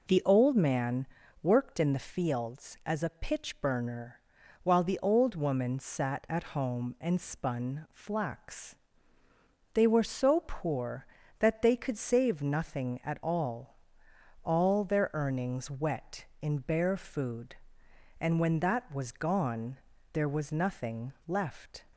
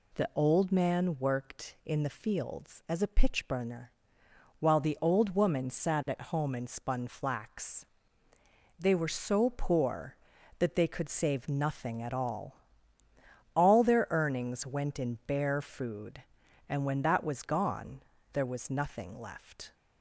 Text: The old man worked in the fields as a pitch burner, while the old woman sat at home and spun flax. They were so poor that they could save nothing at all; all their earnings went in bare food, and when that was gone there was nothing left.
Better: second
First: pauses between "man" and "worked"; at 1.0 s; 0.38 s long // says "wet" for "went"; at 15.6 s // pauses between "gone" and "there"; slight; at 19.7 s; 0.36 s long // pauses between "nothing" and "left"; slight; at 21.1 s; 0.16 s long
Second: pauses between "gone" and "there"; slight; at 18.0 s; 0.30 s long

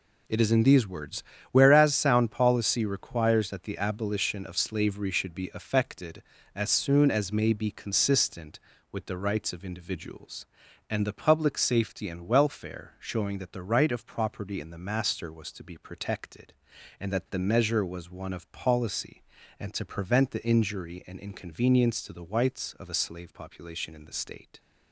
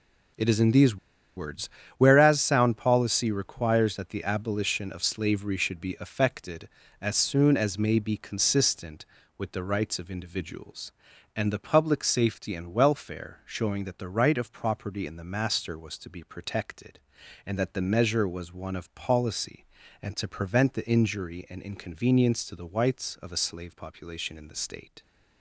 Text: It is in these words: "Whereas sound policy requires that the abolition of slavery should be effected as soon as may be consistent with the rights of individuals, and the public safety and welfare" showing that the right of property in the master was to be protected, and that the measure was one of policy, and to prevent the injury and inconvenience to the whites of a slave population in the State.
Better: first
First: none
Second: pauses between "these" and "words"; at 0.9 s; 0.40 s long

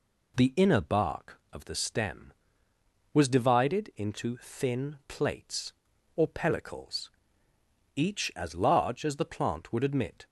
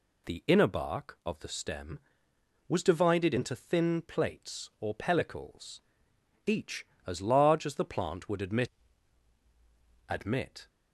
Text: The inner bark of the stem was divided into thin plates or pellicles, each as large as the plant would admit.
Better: first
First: none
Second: says "admit" twice; at 10.0 s

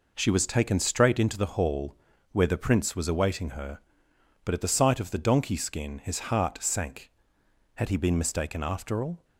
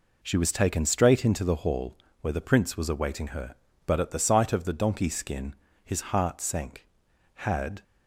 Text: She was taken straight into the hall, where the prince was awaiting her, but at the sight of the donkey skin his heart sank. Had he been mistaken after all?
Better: first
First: none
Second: pauses between "skin" and "his"; slight; at 5.5 s; 0.30 s long // stops before "he been mistaken after all"; at 7.8 s

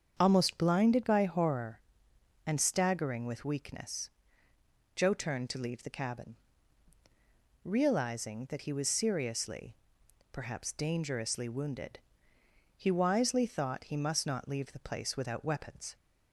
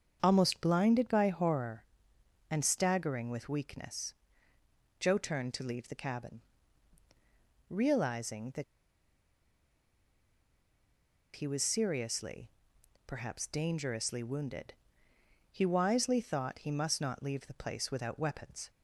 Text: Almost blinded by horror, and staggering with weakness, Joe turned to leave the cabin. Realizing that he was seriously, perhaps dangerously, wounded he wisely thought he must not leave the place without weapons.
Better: first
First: starts louder than the rest; until 1.2 s; 7 dB // pauses between "wounded" and "he"; noticeable; at 11.9 s; 0.78 s long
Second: starts louder than the rest; until 1.2 s; 7 dB // pauses between "that" and "he"; strong; at 8.6 s; 2.7 s long // pauses between "wounded" and "he"; noticeable; at 14.7 s; 0.78 s long

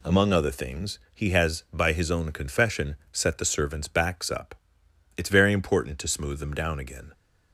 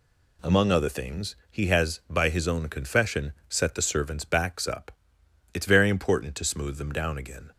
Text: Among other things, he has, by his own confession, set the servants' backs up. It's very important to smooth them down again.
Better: neither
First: none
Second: none

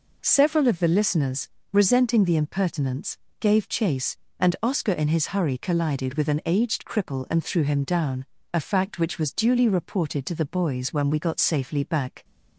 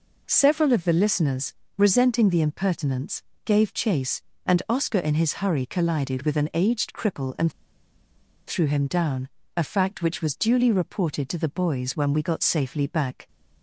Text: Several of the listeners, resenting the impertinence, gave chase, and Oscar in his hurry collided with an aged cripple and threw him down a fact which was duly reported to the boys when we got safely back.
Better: first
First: pauses between "down" and "a"; slight; at 8.2 s; 0.26 s long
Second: pauses between "and" and "threw"; noticeable; at 7.5 s; 0.95 s long // pauses between "down" and "a"; slight; at 9.2 s; 0.26 s long

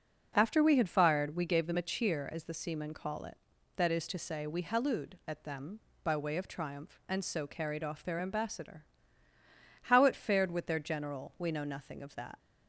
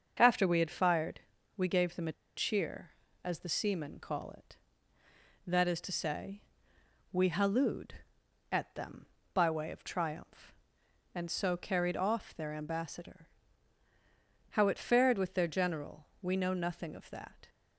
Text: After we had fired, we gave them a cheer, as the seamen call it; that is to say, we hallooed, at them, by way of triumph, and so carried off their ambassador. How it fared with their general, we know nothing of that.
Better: first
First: none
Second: starts louder than the rest; until 1.1 s; 6.5 dB // pauses between "a" and "cheer"; slight; at 2.1 s; 0.23 s long

